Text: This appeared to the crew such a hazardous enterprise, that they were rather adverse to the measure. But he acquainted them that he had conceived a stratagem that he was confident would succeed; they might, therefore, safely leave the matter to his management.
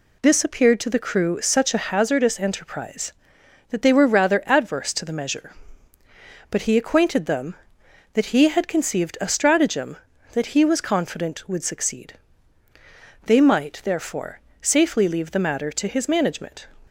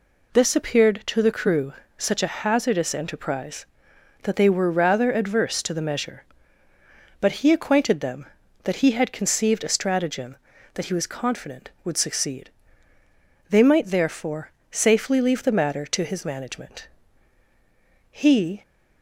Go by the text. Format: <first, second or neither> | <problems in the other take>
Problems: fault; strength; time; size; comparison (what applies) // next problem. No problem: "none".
first | pauses between "crew" and "such"; slight; at 1.7 s; 0.26 s long // goes on to say "He"; from 18.1 s on; 0.50 s long